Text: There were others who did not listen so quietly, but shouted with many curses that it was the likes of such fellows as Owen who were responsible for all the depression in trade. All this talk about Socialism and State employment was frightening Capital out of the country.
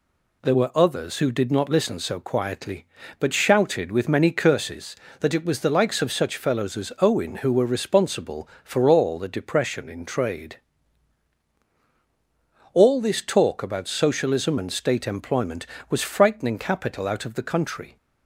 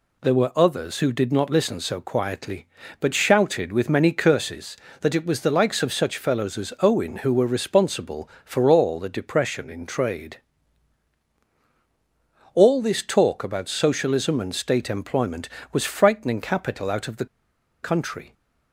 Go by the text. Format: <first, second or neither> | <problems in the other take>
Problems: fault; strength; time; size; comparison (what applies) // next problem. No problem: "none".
first | pauses between "the" and "country"; noticeable; at 17.2 s; 0.56 s long